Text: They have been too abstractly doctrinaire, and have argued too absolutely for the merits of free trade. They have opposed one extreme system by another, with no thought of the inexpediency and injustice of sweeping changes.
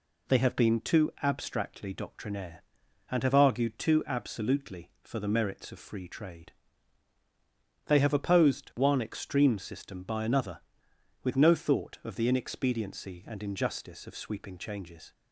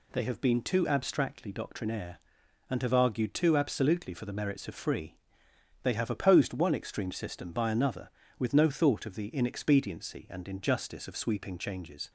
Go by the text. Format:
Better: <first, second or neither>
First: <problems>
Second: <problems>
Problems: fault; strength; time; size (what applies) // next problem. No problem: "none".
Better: first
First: none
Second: skips "trade"; at 5.4 s